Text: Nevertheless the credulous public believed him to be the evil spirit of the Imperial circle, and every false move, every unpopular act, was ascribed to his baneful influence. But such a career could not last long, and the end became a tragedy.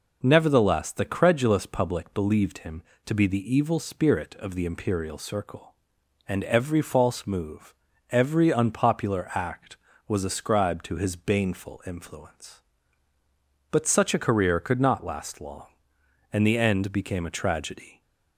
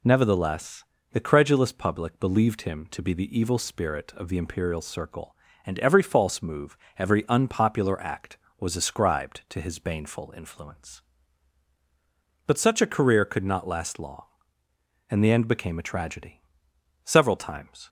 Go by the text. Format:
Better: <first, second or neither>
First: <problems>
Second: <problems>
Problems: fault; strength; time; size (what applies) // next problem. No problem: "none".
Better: first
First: none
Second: pauses between "Nevertheless" and "the"; slight; at 0.8 s; 0.26 s long // goes on to say "Several times"; noticeable; from 17.0 s on; 0.84 s long